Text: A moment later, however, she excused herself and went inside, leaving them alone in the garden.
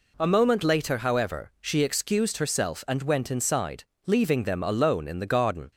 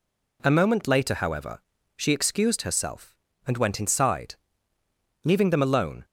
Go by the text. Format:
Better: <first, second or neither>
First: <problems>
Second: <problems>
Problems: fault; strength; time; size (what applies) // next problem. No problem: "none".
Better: first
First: none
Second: stops before "in the garden"; at 6.0 s